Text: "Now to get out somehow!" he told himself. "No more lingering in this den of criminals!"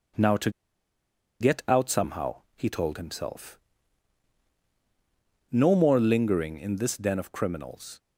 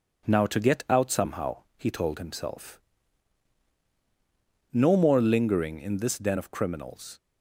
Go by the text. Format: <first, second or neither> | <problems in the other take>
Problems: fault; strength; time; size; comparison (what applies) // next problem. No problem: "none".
second | pauses between "to" and "get"; noticeable; at 0.4 s; 0.90 s long